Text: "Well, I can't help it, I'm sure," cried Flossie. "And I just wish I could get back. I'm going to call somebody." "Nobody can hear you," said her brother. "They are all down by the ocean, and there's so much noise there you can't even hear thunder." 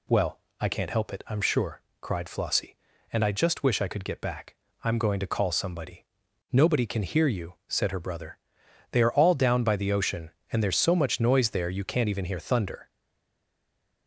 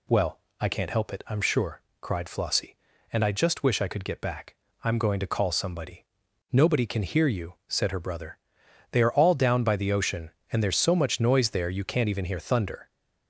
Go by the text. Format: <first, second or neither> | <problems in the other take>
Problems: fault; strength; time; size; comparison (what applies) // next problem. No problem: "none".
second | stays silent after the last word; noticeable; from 12.8 s on; 1.2 s long